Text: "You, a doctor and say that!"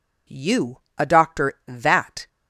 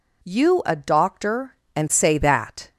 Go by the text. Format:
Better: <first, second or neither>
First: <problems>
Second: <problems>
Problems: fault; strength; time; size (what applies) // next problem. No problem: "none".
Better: second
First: skips "and say"; at 1.5 s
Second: none